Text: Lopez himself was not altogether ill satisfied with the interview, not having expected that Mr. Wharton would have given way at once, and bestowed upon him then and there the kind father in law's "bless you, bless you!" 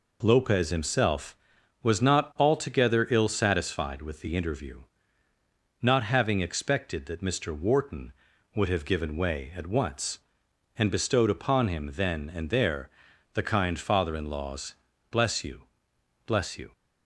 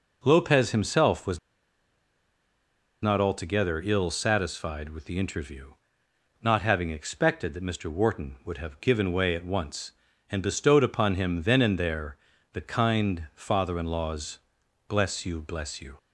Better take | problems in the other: first | pauses between "was" and "not"; strong; at 1.3 s; 1.6 s long // pauses between "there" and "the"; at 12.1 s; 0.38 s long; also in the first // pauses between "law's" and "bless"; noticeable; at 14.3 s; 0.48 s long; slight in the first

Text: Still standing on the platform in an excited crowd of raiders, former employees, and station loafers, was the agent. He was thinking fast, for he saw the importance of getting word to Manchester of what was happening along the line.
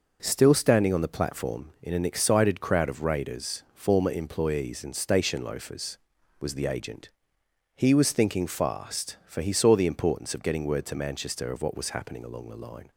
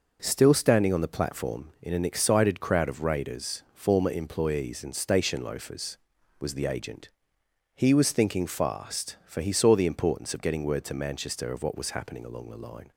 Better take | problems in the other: neither | none

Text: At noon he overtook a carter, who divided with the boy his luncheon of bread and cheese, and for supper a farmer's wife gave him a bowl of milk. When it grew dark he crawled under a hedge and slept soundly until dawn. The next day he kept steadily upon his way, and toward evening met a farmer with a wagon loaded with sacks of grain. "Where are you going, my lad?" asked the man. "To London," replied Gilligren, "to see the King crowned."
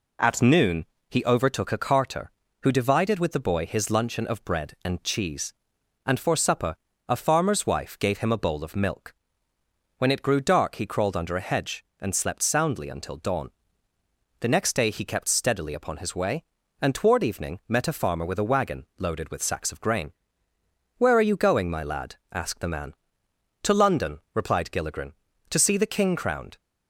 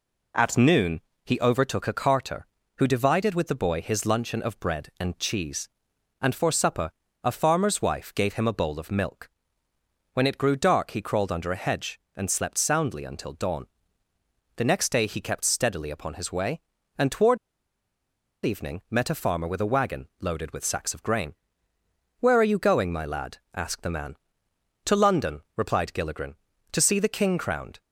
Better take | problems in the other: first | pauses between "noon" and "he"; slight; at 0.9 s; 0.24 s long; slight in the first // pauses between "supper" and "a"; slight; at 6.8 s; 0.34 s long; slight in the first // pauses between "toward" and "evening"; at 17.3 s; 1.0 s long

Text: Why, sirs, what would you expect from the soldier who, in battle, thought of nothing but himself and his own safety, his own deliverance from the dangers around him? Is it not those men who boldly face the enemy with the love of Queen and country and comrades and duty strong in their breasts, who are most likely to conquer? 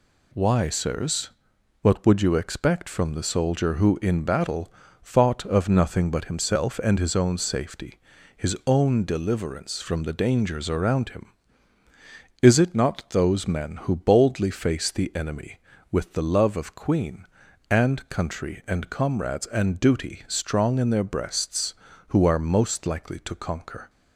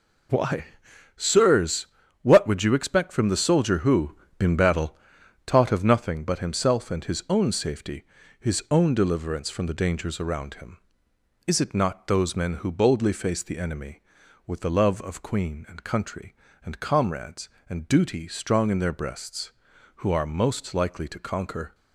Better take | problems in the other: first | says "taught" for "thought"; at 5.4 s

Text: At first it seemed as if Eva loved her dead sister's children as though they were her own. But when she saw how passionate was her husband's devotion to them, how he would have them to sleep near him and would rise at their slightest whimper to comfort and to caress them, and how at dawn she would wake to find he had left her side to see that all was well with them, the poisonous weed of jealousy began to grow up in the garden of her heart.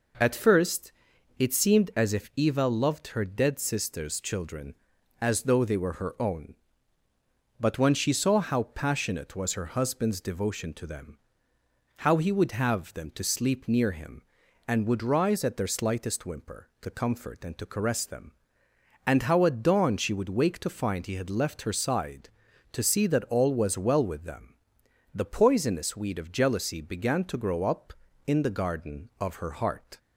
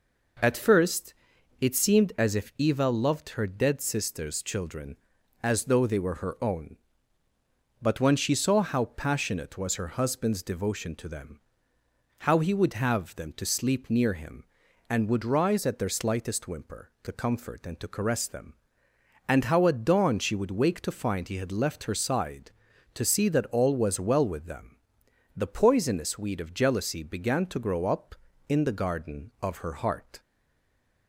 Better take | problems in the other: first | pauses between "first" and "it"; noticeable; at 1.1 s; 0.46 s long; noticeable in the first // stays silent after the last word; slight; from 30.1 s on; 0.9 s long

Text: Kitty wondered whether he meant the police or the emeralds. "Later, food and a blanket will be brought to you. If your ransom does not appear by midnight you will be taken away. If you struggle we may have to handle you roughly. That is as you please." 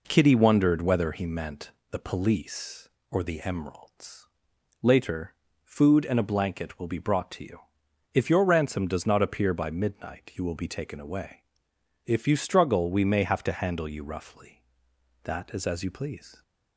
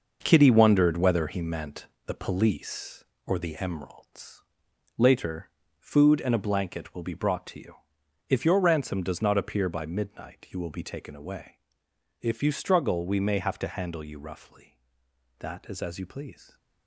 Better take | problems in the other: first | gets quieter; strong; throughout; 8 dB // pauses between "meant" and "the"; slight; at 1.8 s; 0.18 s long; slight in the first

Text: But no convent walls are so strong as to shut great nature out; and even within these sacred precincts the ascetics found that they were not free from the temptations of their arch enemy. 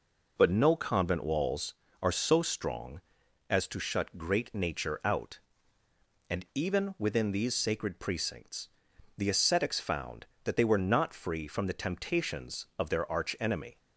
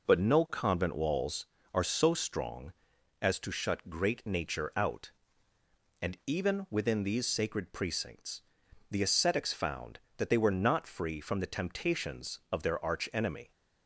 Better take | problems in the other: neither | pauses between "precincts" and "the"; noticeable; the same in both

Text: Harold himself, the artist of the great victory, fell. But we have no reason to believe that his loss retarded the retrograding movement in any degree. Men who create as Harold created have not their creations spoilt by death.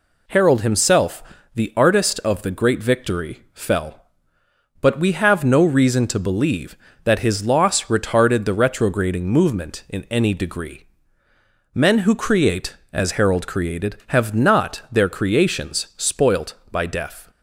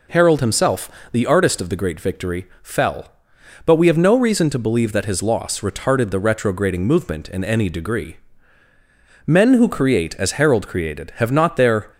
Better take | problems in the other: first | stops before "creations spoilt by death"; at 11.9 s

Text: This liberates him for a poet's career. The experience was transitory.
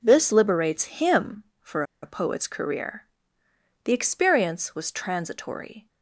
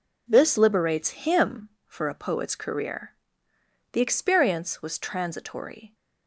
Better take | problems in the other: second | pauses between "for" and "a"; slight; at 1.8 s; 0.19 s long

